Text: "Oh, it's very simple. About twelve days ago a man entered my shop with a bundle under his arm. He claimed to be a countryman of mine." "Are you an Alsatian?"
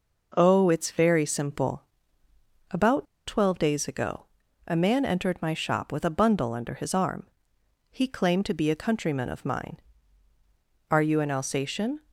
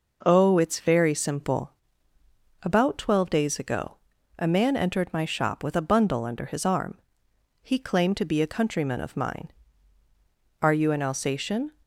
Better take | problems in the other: second | pauses between "About" and "twelve"; slight; at 3.0 s; 0.21 s long // pauses between "ago" and "a"; at 4.2 s; 0.40 s long; also in the second

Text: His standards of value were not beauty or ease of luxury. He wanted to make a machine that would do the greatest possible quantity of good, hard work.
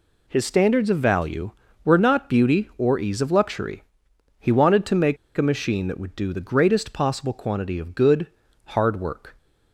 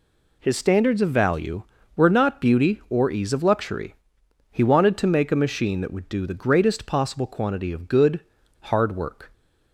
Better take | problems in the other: second | pauses between "make" and "a"; slight; at 5.1 s; 0.21 s long

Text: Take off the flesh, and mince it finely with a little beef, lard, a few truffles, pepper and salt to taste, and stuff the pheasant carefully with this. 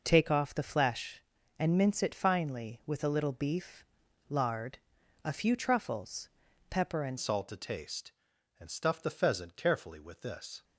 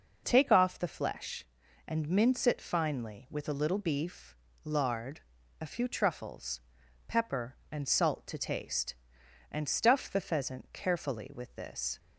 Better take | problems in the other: second | changes voice at "salt"; from 7.1 s on; 3.5 s long

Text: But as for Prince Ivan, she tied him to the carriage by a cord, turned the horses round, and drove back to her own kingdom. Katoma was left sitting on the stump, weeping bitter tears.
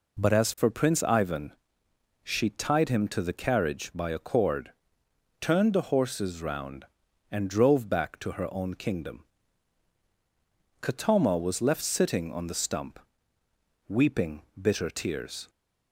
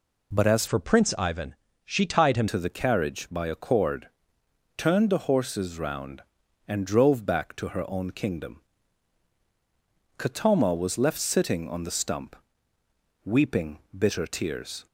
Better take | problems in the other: first | changes voice from "for" to "him"; from 0.6 to 2.4 s; 1.8 s long

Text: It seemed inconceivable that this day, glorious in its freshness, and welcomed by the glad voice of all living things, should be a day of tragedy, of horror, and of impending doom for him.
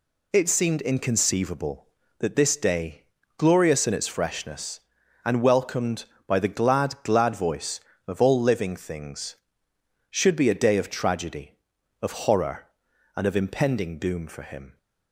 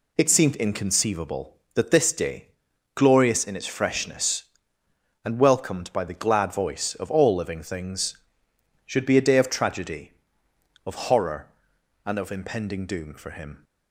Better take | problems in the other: second | says "glad" twice; at 7.0 s

